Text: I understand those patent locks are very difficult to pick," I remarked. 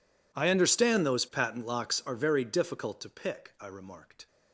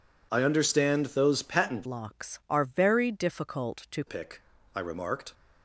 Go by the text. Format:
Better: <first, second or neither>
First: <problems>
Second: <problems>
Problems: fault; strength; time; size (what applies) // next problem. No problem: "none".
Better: first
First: none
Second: changes voice from "locks" to "to"; from 1.8 to 4.0 s; 2.2 s long